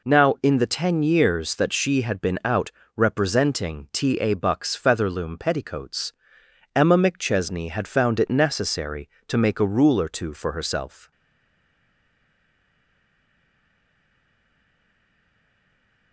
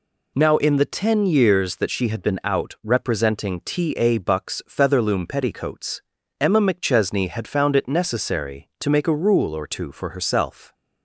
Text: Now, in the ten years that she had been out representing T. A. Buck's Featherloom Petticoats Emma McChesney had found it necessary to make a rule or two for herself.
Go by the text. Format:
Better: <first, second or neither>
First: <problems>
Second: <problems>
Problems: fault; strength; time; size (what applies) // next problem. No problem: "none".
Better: second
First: pauses between "out" and "representing"; slight; at 2.7 s; 0.26 s long // pauses between "Petticoats" and "Emma"; noticeable; at 6.1 s; 0.62 s long // stays silent after the last word; strong; from 11.1 s on; 5.0 s long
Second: pauses between "Petticoats" and "Emma"; at 6.0 s; 0.40 s long